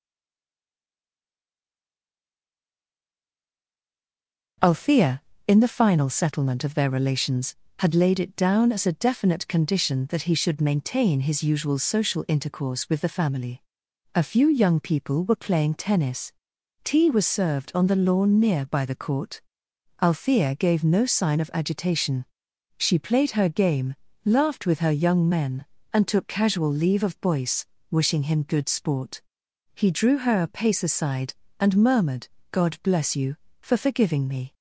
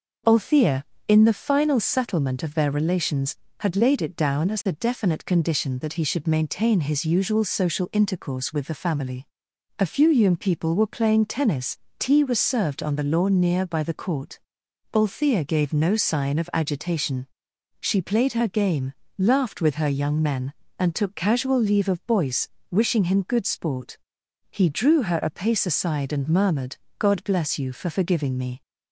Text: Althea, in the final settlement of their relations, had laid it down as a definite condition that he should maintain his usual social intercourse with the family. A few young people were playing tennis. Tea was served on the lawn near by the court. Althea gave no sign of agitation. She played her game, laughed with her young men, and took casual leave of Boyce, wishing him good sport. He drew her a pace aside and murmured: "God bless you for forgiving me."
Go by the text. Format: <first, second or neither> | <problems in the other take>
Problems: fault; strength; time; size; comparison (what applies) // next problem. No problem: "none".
second | stays silent before the first word; strong; until 4.5 s; 4.5 s long